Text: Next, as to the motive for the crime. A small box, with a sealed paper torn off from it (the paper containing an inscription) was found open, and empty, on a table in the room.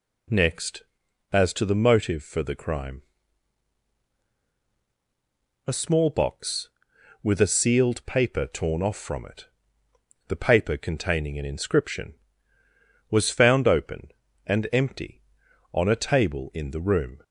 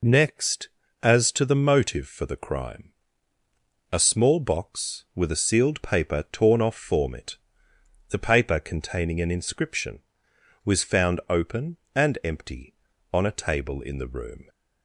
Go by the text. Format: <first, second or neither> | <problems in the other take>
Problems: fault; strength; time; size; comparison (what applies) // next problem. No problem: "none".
first | says "form" for "from"; at 6.7 s